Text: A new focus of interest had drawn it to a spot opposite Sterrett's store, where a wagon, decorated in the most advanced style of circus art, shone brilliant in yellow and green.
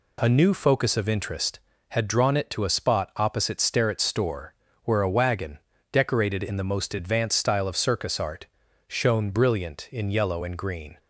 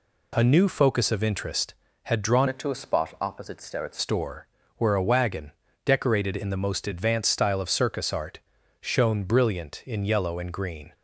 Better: first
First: none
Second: changes voice from "it" to "Sterrett's"; from 2.4 to 3.9 s; 1.5 s long

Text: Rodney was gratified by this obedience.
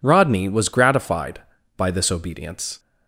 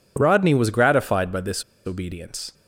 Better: first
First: none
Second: pauses between "this" and "obedience"; slight; at 1.6 s; 0.22 s long

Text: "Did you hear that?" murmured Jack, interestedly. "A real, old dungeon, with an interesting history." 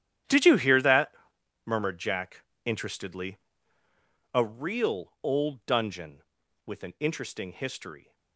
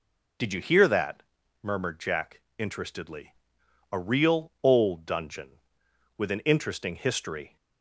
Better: second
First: gets quieter; strong; throughout; 16 dB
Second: none

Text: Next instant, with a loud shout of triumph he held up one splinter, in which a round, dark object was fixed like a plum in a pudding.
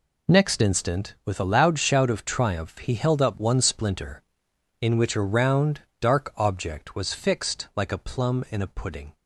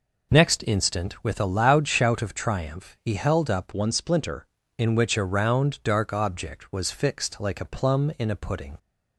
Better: first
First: none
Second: changes voice from "one" to "splinter"; from 3.7 to 4.4 s; 0.7 s long

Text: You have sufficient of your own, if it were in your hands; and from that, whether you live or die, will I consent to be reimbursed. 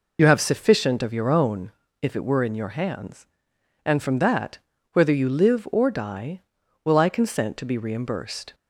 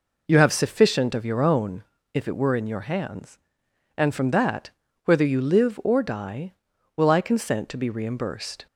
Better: second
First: loses the start of "You"; at 0.1 s; 30 ms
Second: none

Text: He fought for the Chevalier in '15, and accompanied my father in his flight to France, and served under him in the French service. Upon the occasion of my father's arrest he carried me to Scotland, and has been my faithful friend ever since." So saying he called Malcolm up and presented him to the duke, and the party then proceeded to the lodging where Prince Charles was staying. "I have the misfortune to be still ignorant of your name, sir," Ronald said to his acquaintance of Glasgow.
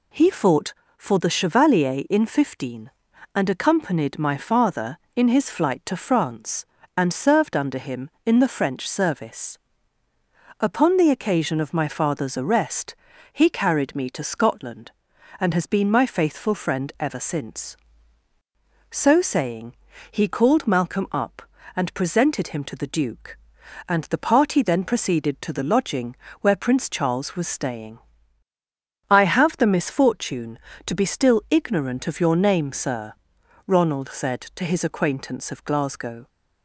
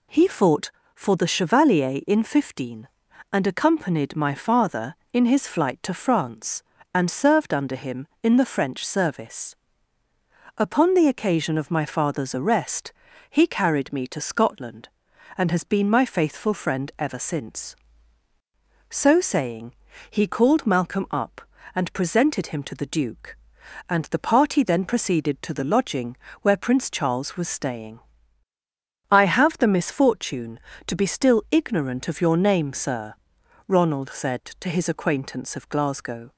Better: neither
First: pauses between "arrest" and "he"; at 12.9 s; 0.38 s long // pauses between "saying" and "he"; slight; at 19.7 s; 0.34 s long // pauses between "lodging" and "where"; slight; at 26.1 s; 0.24 s long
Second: pauses between "arrest" and "he"; at 12.9 s; 0.38 s long // pauses between "saying" and "he"; slight; at 19.7 s; 0.34 s long // pauses between "lodging" and "where"; slight; at 26.1 s; 0.24 s long

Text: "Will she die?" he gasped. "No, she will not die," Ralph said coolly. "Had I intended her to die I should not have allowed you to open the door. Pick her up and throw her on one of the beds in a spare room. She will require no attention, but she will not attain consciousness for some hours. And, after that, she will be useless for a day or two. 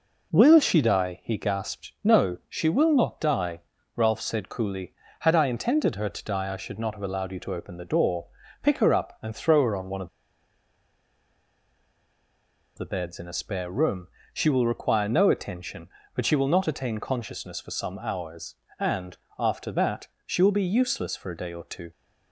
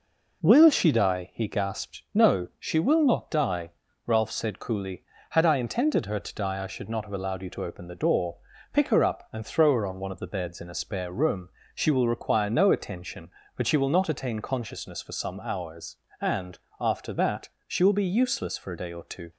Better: second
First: pauses between "of" and "the"; strong; at 10.0 s; 2.7 s long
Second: none

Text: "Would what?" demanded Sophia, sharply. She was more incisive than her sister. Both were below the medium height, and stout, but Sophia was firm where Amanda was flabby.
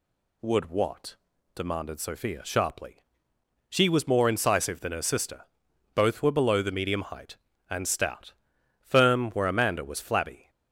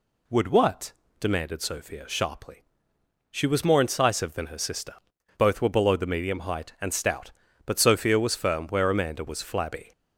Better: second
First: skips "but Sophia was"; at 8.5 s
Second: none

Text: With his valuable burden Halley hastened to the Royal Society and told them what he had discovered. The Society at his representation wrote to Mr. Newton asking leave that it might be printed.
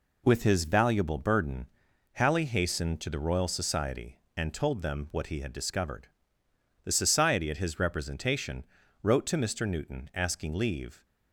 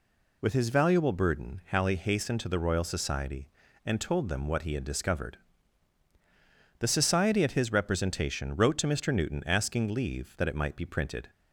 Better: second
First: pauses between "burden" and "Halley"; noticeable; at 1.6 s; 0.46 s long // pauses between "representation" and "wrote"; at 8.6 s; 0.38 s long // stops before "that it might be printed"; at 11.0 s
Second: none

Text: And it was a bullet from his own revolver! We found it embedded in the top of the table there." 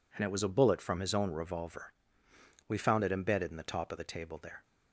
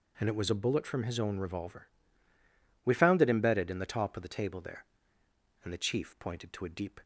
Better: first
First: none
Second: goes on to say "And the chief pointed to a deep"; from 5.6 s on; 1.3 s long

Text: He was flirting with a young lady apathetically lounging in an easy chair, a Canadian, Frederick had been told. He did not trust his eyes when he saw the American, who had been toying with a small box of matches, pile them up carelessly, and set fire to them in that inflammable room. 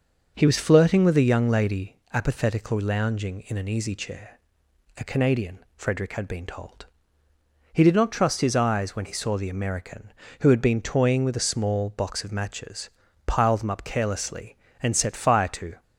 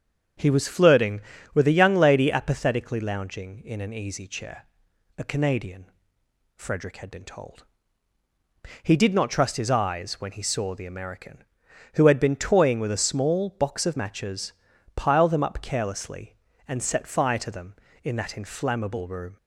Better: second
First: starts louder than the rest; until 1.3 s; 6.5 dB // pauses between "lady" and "apathetically"; slight; at 1.9 s; 0.17 s long // stops before "them in that inflammable room"; at 15.8 s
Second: starts louder than the rest; strong; until 1.7 s; 7.5 dB

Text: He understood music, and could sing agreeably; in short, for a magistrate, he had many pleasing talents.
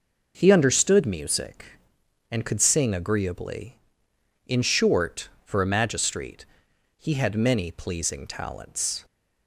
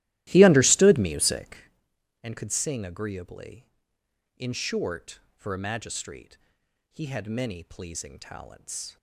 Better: first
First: none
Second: starts louder than the rest; strong; until 1.7 s; 15.5 dB

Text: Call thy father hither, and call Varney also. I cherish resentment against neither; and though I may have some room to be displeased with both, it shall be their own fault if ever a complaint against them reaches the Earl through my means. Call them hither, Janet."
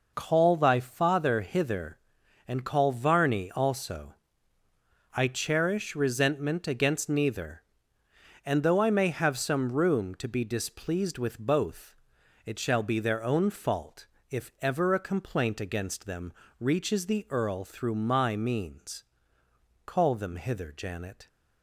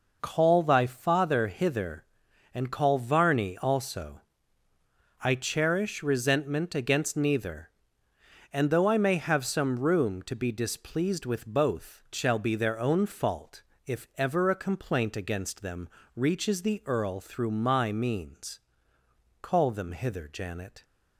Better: first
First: pauses between "fault" and "if"; slight; at 14.0 s; 0.24 s long // pauses between "them" and "reaches"; slight; at 16.3 s; 0.28 s long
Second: skips "it"; at 12.0 s // pauses between "fault" and "if"; slight; at 13.6 s; 0.24 s long // pauses between "them" and "reaches"; slight; at 15.8 s; 0.28 s long

